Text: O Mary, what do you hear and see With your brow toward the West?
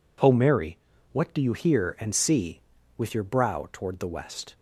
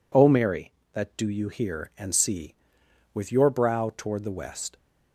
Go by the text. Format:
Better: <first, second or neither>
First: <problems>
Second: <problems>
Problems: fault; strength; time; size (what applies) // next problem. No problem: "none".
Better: first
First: none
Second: says "that" for "what"; at 0.9 s